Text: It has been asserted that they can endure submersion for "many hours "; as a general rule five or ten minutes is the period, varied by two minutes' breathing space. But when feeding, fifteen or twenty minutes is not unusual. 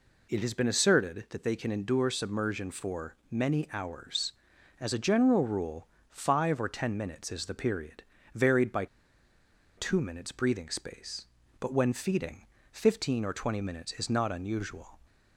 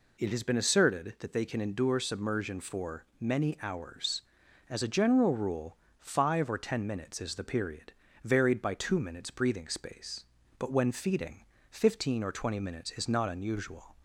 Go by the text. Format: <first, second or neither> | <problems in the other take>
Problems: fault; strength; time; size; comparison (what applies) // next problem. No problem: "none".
second | pauses between "for" and "many"; slight; at 3.1 s; 0.16 s long; slight in the second // pauses between "rule" and "five"; slight; at 5.8 s; 0.24 s long; slight in the second // pauses between "by" and "two"; noticeable; at 8.8 s; 0.91 s long